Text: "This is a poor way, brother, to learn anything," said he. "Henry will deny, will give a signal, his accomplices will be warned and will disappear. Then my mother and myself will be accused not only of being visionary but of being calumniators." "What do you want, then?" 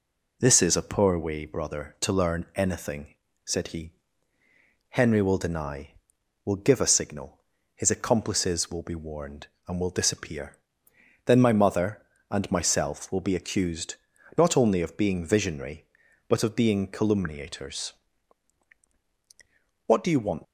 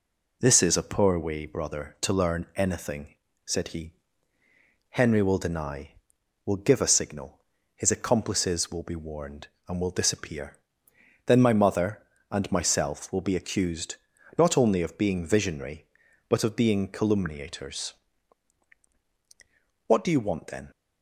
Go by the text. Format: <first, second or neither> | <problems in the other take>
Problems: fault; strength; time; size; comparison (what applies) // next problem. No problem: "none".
second | pauses between "accused" and "not"; at 13.9 s; 0.42 s long; also in the second // stops before "then"; at 20.4 s